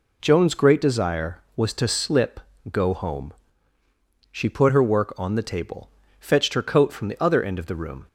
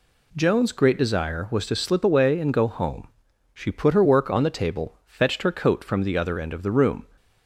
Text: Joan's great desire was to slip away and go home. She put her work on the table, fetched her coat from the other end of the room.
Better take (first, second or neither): second